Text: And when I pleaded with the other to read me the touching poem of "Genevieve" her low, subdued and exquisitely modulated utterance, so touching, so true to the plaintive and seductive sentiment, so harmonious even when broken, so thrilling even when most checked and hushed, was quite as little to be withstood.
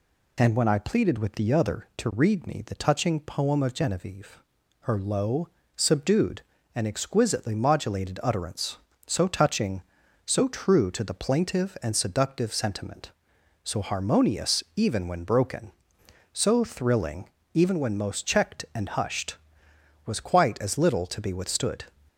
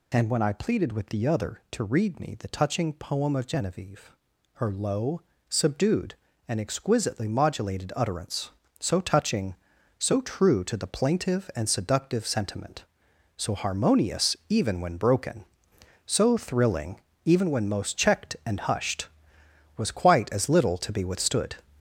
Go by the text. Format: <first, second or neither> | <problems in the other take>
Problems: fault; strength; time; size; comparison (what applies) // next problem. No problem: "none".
first | gets louder; throughout; 6 dB // pauses between "Genevieve" and "her"; noticeable; at 4.1 s; 0.46 s long; noticeable in the first // pauses between "thrilling" and "even"; slight; at 16.9 s; 0.24 s long; slight in the first